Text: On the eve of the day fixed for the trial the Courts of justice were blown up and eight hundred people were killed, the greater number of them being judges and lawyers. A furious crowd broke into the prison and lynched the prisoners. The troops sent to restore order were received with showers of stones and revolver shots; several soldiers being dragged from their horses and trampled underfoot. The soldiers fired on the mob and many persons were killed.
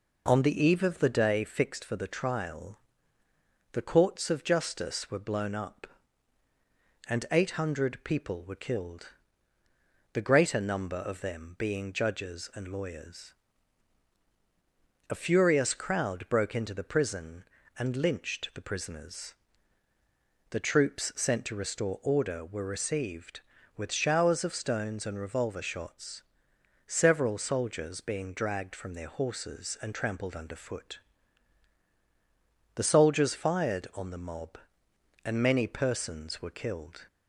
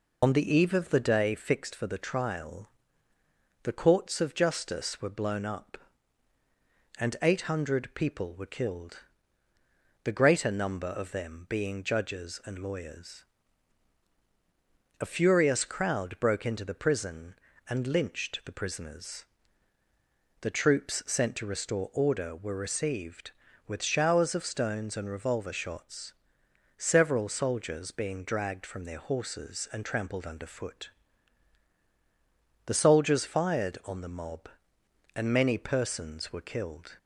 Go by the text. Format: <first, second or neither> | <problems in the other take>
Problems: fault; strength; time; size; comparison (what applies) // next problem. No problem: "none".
first | loses the start of "On"; at 0.2 s; 60 ms // pauses between "trial" and "the"; noticeable; at 2.6 s; 0.92 s long; noticeable in the first